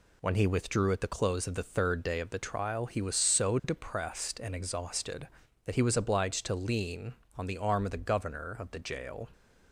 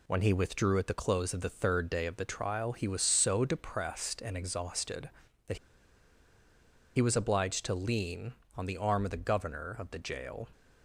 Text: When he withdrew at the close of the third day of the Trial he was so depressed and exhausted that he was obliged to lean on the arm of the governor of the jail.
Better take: first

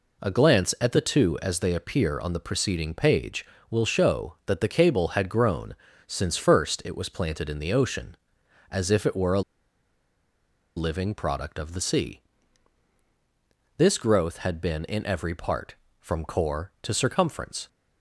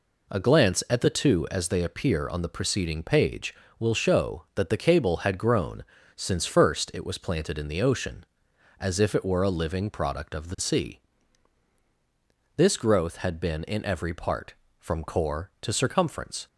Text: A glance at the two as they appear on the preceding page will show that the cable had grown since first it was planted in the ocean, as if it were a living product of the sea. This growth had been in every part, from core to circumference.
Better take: second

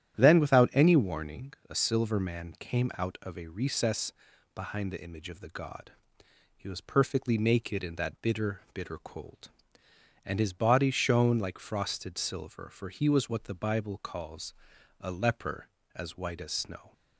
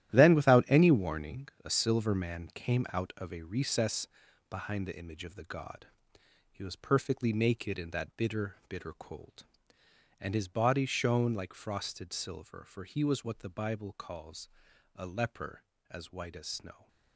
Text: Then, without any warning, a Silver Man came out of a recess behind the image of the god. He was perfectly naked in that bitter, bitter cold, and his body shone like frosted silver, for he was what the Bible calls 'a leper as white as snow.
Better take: first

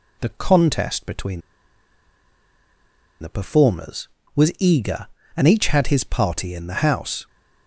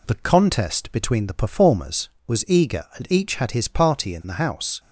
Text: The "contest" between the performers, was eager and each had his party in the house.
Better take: second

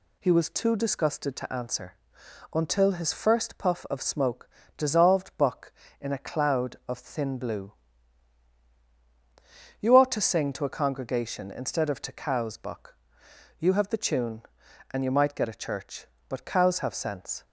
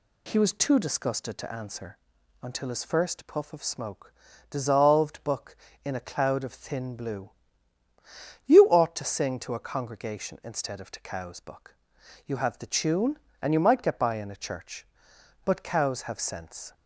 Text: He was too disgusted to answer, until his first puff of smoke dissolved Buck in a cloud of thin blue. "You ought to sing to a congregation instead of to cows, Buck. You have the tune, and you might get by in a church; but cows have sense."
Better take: second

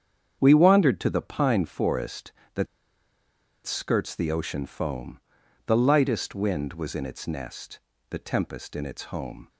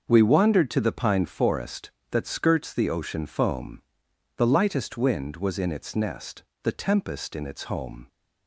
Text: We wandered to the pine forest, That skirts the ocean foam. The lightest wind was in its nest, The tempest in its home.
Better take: second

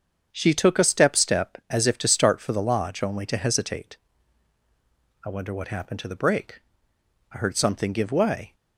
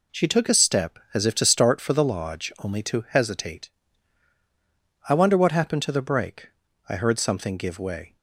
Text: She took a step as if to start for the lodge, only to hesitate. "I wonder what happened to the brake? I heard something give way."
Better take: second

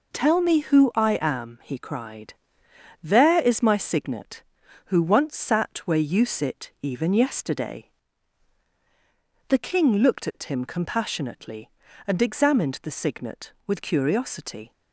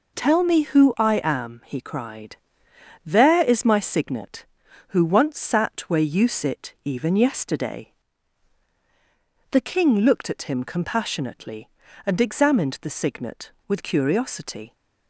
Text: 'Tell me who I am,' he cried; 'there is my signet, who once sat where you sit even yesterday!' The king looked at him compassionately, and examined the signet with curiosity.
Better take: neither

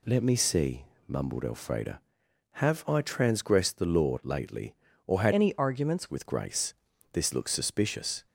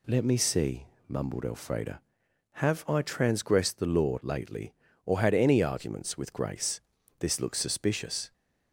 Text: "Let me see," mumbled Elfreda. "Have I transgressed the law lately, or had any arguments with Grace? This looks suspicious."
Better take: second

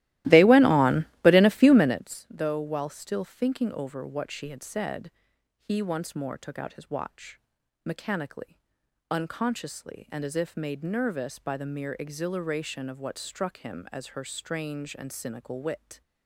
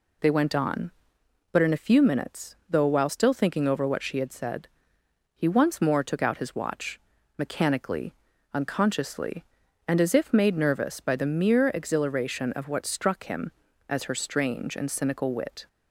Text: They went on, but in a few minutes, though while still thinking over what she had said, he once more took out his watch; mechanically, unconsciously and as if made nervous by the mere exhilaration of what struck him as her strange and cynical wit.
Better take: second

